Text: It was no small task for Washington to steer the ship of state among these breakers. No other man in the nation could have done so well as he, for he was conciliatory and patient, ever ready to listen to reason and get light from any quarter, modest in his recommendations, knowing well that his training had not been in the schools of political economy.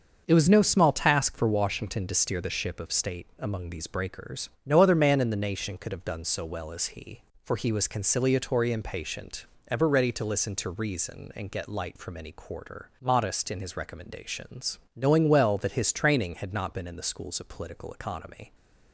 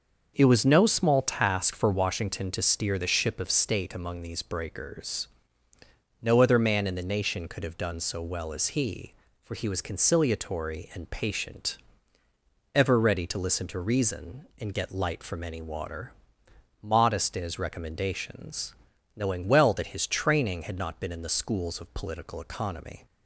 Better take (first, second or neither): first